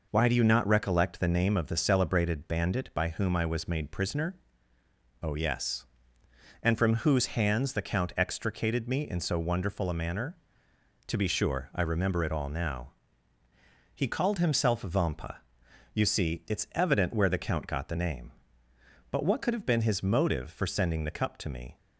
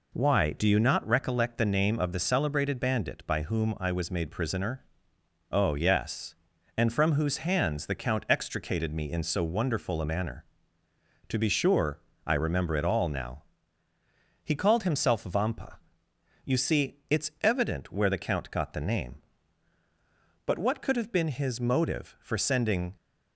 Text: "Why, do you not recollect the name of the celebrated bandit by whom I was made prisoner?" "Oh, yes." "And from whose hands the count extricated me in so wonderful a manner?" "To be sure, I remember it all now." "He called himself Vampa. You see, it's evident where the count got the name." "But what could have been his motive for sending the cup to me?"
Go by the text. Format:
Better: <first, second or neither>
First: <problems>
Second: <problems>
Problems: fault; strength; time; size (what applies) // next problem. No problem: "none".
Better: first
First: none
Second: stops before "the cup to me"; at 22.9 s